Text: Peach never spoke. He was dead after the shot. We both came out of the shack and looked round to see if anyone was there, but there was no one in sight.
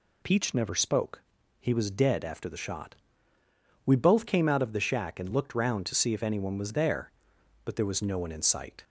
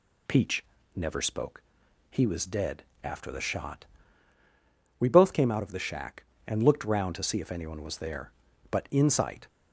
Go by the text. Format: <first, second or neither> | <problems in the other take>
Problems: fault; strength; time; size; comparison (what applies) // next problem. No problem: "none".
first | pauses between "Peach" and "never"; slight; at 0.6 s; 0.32 s long // pauses between "dead" and "after"; slight; at 2.8 s; 0.20 s long // skips "there was no one"; at 8.8 s